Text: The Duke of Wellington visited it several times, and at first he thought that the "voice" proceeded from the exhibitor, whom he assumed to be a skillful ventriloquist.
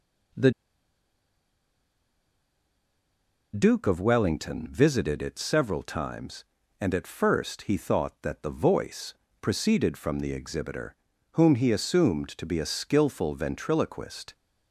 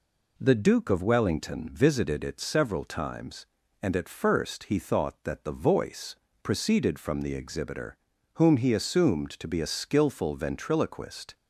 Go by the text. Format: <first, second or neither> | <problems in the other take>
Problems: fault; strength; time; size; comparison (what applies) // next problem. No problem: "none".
second | pauses between "The" and "Duke"; strong; at 0.5 s; 3.0 s long // pauses between "voice" and "proceeded"; slight; at 9.1 s; 0.26 s long; slight in the second